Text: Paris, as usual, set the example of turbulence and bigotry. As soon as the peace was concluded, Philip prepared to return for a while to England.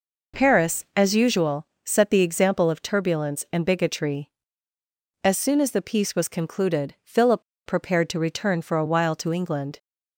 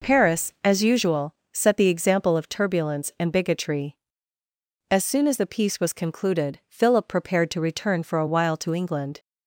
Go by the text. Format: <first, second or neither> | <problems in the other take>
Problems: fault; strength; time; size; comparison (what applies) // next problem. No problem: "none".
second | pauses between "Philip" and "prepared"; slight; at 7.4 s; 0.25 s long